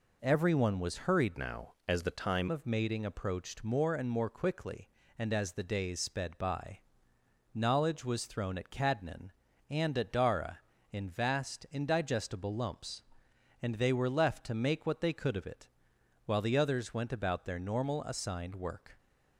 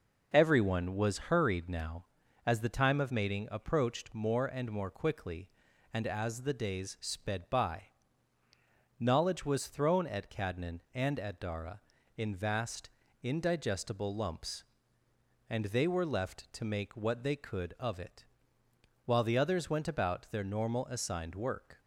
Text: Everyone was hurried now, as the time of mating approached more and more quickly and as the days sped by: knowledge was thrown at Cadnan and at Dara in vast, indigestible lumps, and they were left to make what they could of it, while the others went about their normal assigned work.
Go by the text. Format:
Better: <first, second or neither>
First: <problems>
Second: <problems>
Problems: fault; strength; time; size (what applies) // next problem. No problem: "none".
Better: second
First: changes voice from "now" to "time"; from 1.3 to 2.4 s; 1.1 s long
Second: none